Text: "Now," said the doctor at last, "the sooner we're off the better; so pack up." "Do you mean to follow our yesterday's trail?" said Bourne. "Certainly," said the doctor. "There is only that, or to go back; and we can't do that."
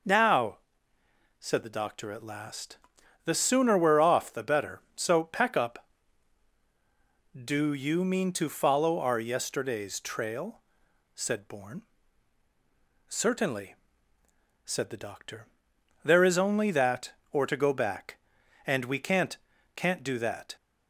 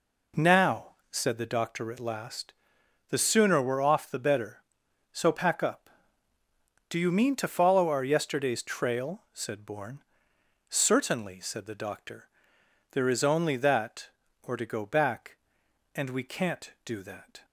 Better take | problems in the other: second | says "can't" twice; at 19.7 s

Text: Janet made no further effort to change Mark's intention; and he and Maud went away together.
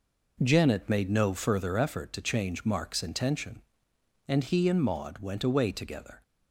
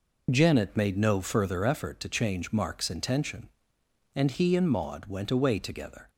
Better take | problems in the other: first | loses the start of "Janet"; at 0.2 s; 30 ms

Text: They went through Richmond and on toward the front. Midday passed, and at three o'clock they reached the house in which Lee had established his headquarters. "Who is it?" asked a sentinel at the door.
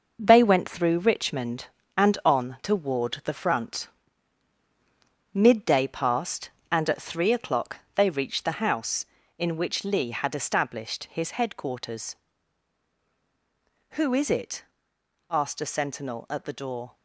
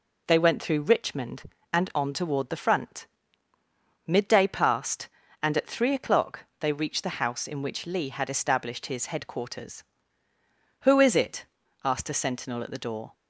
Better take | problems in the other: second | gets quieter; strong; throughout; 7.5 dB // pauses between "o'clock" and "they"; slight; at 7.7 s; 0.18 s long; slight in the second

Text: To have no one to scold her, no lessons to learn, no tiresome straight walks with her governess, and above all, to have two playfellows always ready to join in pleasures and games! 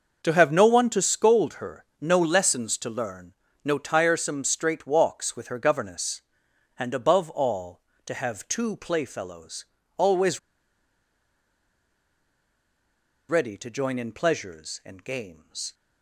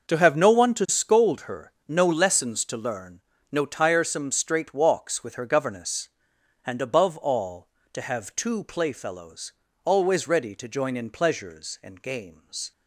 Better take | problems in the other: second | starts louder than the rest; until 1.2 s; 6.5 dB; also in the second // pauses between "playfellows" and "always"; slight; at 9.6 s; 0.32 s long; slight in the second // pauses between "always" and "ready"; strong; at 10.3 s; 2.9 s long

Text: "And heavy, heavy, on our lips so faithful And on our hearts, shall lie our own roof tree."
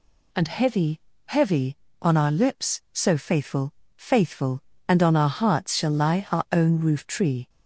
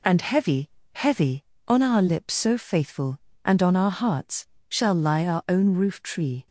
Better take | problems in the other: second | says "faithful" twice; at 3.9 s

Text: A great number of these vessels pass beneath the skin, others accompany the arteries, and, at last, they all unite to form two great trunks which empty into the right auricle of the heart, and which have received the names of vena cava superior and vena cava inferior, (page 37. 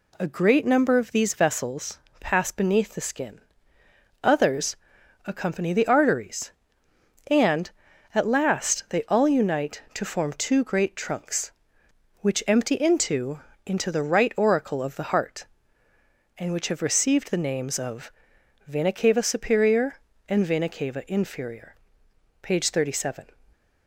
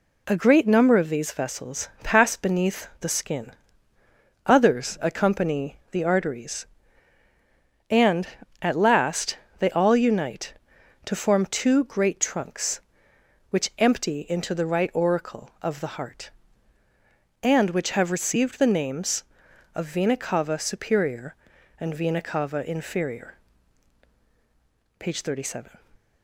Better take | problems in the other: second | pauses between "vessels" and "pass"; slight; at 1.9 s; 0.22 s long; slight in the second // pauses between "others" and "accompany"; noticeable; at 4.7 s; 0.50 s long // says "into" twice; at 13.6 s // pauses between "of" and "vena"; noticeable; at 18.1 s; 0.56 s long

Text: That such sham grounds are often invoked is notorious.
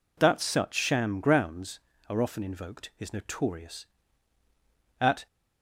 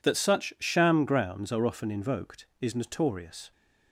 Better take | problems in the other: second | goes on to say "At"; slight; from 5.0 s on; 0.26 s long

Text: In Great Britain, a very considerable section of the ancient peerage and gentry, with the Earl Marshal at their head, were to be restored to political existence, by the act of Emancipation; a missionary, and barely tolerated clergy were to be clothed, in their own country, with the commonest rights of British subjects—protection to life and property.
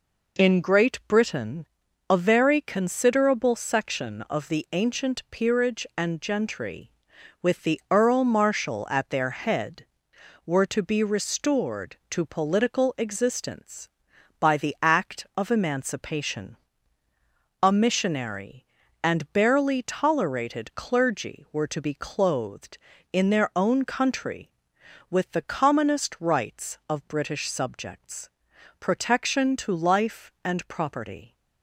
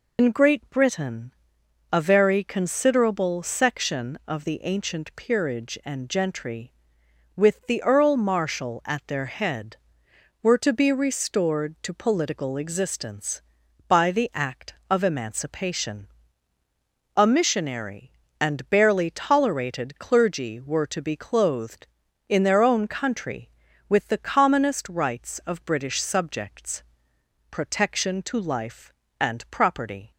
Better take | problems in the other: first | loses the start of "In"; at 0.1 s; 90 ms

